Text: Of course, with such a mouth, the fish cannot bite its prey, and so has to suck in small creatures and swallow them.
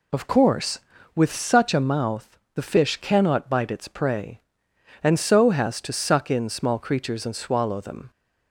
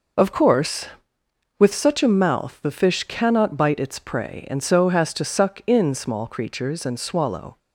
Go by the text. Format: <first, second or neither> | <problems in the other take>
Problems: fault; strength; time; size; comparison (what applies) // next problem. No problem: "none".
first | stops before "them"; at 7.5 s